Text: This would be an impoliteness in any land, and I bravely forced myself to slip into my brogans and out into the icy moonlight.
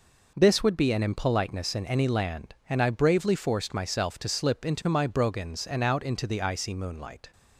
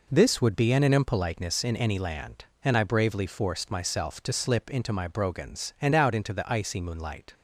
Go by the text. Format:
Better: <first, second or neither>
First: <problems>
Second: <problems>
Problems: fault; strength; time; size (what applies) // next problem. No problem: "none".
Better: first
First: none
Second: says "an" twice; at 0.8 s